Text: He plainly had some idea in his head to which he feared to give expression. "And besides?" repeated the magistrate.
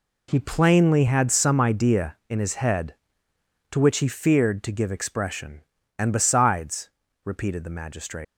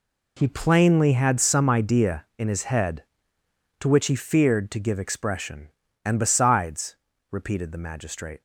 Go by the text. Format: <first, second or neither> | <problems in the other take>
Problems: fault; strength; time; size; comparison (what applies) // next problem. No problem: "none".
second | leaves "magistrate" unfinished; at 8.2 s; 85 ms